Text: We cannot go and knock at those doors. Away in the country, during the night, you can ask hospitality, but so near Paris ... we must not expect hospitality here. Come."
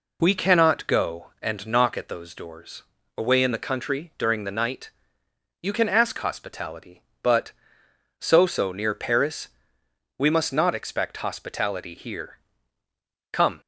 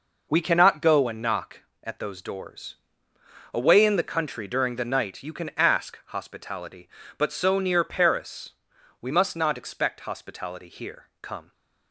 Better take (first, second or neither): second